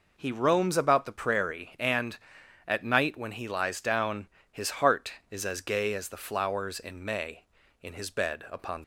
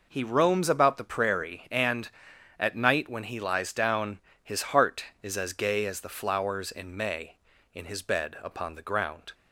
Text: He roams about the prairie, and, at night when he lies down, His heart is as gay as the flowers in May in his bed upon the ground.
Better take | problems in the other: second | stops before "the ground"; at 8.8 s

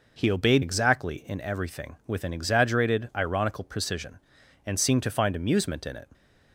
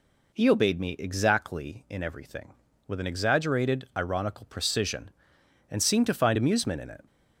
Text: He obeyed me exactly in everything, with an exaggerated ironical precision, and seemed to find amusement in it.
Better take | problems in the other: second | skips "me"; at 0.6 s

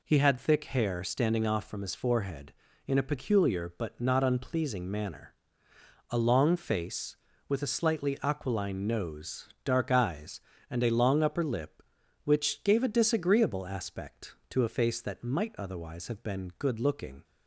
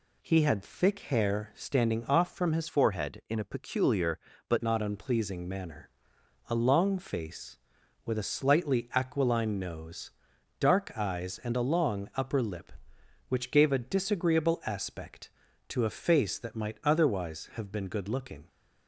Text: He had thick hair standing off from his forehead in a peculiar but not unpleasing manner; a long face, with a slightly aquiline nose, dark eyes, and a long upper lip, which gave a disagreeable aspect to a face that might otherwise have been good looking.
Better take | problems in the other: first | changes voice from "forehead" to "but"; from 2.6 to 4.6 s; 2.0 s long

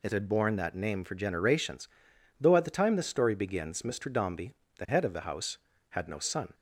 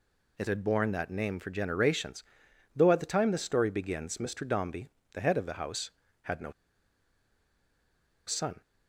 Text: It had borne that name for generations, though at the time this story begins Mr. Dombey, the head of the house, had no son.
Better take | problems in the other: first | pauses between "no" and "son"; strong; at 6.5 s; 1.7 s long

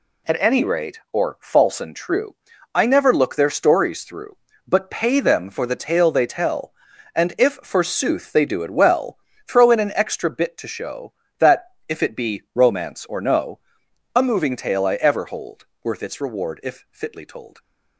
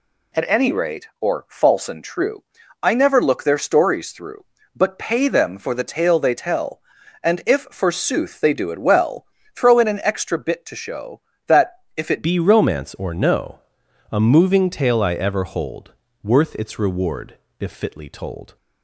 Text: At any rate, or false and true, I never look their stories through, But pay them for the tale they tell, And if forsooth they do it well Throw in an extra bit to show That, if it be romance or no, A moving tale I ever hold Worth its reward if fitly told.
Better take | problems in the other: first | pauses between "well" and "Throw"; slight; at 9.2 s; 0.30 s long; slight in the first // changes voice at "be"; from 12.2 s on; 6.3 s long // pauses between "hold" and "Worth"; slight; at 15.9 s; 0.30 s long; slight in the first // pauses between "reward" and "if"; slight; at 17.3 s; 0.22 s long

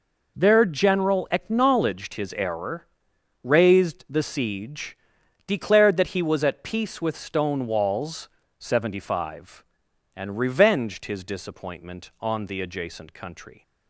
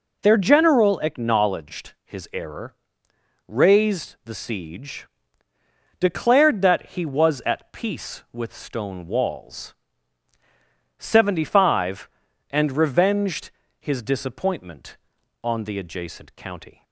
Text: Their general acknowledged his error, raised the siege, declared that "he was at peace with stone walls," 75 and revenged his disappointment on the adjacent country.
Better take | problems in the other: first | pauses between "revenged" and "his"; slight; at 13.4 s; 0.30 s long // says "county" for "country"; at 16.3 s

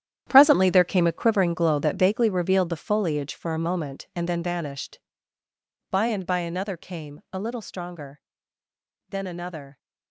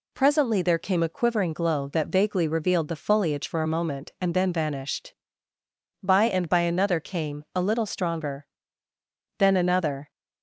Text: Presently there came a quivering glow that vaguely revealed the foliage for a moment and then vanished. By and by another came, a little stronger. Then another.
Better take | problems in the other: second | gets quieter; strong; throughout; 12.5 dB

